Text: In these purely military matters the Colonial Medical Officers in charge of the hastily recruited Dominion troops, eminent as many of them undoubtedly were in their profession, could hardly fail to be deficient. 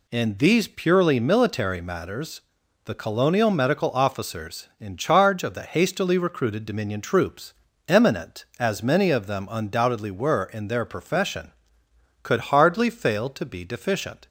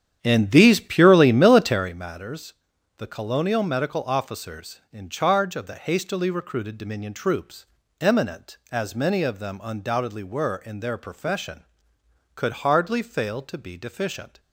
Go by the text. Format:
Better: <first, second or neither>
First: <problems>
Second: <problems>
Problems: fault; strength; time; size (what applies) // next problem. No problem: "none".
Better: first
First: pauses between "matters" and "the"; noticeable; at 2.3 s; 0.46 s long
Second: starts louder than the rest; strong; until 1.9 s; 9.5 dB // pauses between "matters" and "the"; noticeable; at 2.5 s; 0.46 s long